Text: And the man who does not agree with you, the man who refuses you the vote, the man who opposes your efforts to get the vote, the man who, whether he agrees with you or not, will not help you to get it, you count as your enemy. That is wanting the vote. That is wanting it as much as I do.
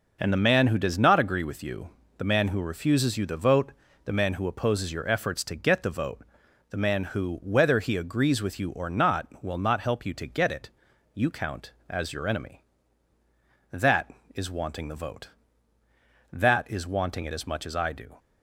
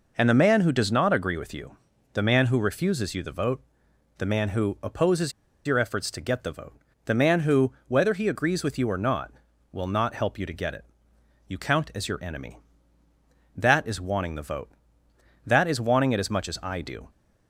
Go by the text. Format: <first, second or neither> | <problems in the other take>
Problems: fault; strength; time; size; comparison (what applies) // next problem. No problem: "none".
first | pauses between "opposes" and "your"; slight; at 5.3 s; 0.34 s long